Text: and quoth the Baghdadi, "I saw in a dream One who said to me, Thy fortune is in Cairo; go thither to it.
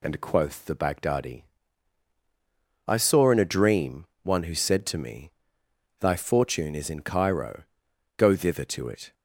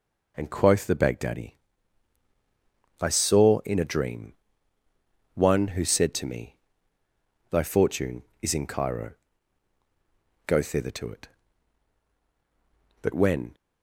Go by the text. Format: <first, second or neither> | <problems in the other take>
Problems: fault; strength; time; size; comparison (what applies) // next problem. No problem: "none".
first | pauses between "dream" and "One"; at 4.3 s; 1.0 s long; slight in the first // goes on to say "But when"; from 13.0 s on; 0.54 s long